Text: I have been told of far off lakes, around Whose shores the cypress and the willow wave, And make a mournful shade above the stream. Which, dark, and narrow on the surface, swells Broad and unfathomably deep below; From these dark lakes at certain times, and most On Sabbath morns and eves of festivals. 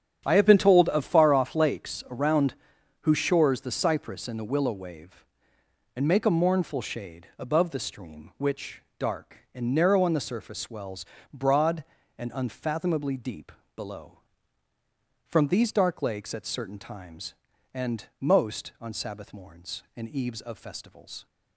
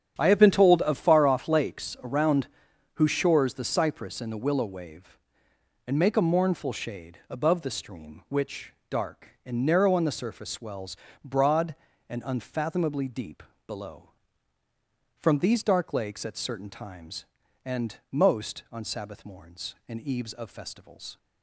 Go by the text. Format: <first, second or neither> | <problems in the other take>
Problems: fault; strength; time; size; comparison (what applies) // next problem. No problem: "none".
neither | starts louder than the rest; strong; the same in both // pauses between "around" and "Whose"; noticeable; the same in both // pauses between "swells" and "Broad"; slight; the same in both // pauses between "deep" and "below"; slight; the same in both // pauses between "and" and "most"; slight; the same in both